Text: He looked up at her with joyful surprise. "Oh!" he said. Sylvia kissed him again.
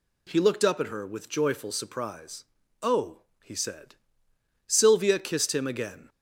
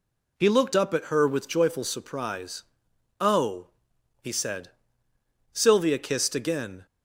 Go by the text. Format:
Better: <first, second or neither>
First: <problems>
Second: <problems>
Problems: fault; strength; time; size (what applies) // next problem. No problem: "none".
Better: first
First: none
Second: skips "him"; at 6.3 s